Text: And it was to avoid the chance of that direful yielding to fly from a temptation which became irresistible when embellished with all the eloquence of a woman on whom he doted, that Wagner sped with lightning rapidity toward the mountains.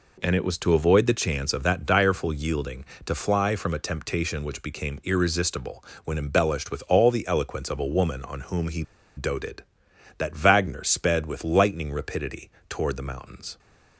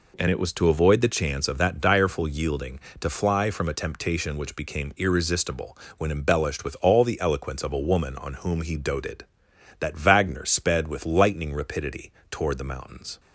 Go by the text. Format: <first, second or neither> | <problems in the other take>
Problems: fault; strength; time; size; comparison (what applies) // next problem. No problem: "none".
second | pauses between "irresistible" and "when"; slight; at 5.8 s; 0.22 s long; slight in the second // pauses between "he" and "doted"; slight; at 8.8 s; 0.34 s long // pauses between "rapidity" and "toward"; slight; at 12.5 s; 0.18 s long; slight in the second